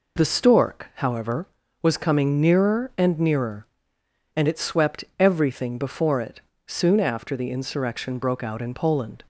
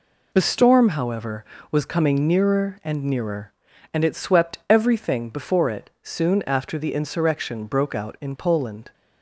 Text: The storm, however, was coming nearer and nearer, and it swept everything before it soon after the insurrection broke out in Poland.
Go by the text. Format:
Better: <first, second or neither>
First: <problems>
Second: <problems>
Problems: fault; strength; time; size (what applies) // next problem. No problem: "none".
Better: second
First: says "stork" for "storm"; at 0.2 s // pauses between "it" and "soon"; slight; at 6.4 s; 0.24 s long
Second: none